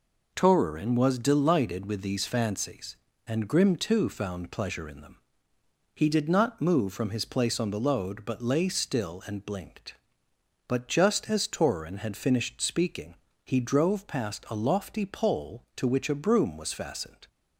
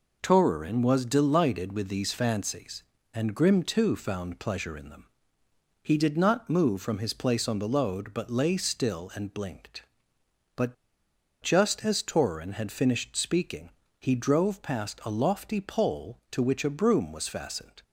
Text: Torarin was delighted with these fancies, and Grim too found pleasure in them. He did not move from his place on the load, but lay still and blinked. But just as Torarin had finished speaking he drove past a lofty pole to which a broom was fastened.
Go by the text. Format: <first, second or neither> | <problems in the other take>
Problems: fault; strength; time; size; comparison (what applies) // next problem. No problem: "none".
first | pauses between "But" and "just"; noticeable; at 10.7 s; 0.67 s long // pauses between "speaking" and "he"; slight; at 13.7 s; 0.28 s long; slight in the first